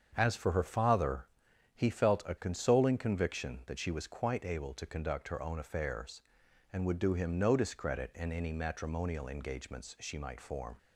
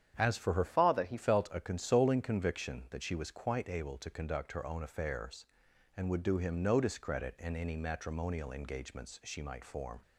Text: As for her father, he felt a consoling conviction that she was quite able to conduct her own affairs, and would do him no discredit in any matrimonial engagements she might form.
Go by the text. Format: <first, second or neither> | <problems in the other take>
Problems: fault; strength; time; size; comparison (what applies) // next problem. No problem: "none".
first | starts louder than the rest; strong; until 1.1 s; 9 dB; strong in the first // changes voice from "father" to "he"; from 0.6 to 1.1 s; 0.5 s long